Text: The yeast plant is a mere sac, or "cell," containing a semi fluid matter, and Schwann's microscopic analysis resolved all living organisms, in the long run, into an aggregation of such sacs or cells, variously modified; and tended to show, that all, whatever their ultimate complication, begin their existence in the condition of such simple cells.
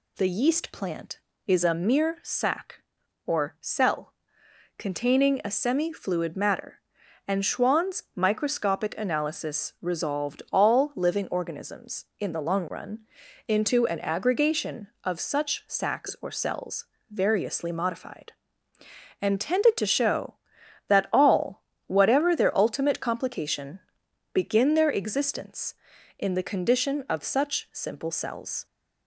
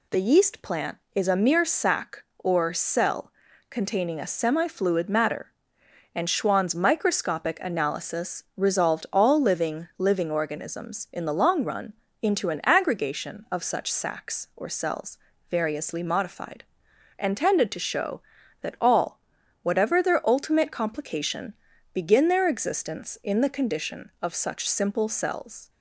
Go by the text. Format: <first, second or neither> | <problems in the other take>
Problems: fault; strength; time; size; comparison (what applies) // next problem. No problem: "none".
first | says "living" twice; at 9.9 s